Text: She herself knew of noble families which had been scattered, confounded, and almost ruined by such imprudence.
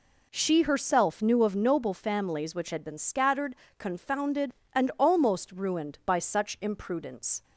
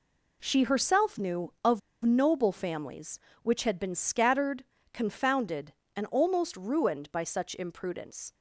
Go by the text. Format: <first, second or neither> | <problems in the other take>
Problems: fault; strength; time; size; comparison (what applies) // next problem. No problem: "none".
first | pauses between "of" and "noble"; slight; at 1.7 s; 0.25 s long